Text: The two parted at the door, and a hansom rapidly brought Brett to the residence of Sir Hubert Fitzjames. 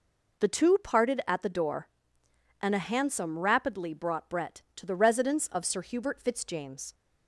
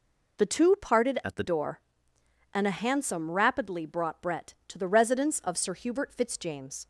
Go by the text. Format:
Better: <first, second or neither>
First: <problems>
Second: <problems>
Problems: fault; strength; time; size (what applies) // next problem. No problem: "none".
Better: first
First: none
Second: changes voice from "at" to "the"; from 1.2 to 1.4 s; 0.2 s long